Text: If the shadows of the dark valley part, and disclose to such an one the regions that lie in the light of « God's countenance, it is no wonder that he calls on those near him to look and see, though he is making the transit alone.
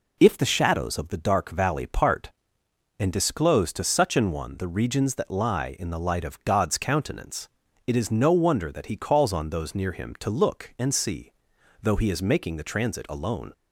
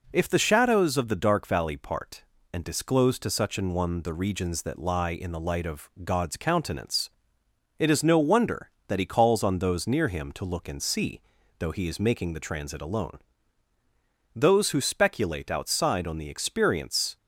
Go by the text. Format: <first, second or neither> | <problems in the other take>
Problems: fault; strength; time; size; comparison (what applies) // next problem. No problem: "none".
first | goes on to say "Those who speculate outside on the experience"; strong; from 14.3 s on; 2.8 s long